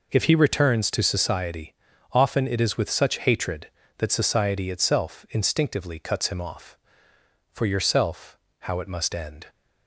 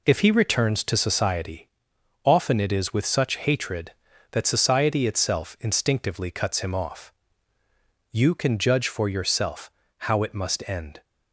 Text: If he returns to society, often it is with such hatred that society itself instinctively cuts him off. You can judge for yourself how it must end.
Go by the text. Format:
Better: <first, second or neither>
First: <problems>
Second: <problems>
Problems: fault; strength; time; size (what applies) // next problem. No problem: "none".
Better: second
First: skips "You can judge"; at 7.1 s // pauses between "yourself" and "how"; slight; at 8.3 s; 0.22 s long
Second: pauses between "yourself" and "how"; slight; at 9.6 s; 0.30 s long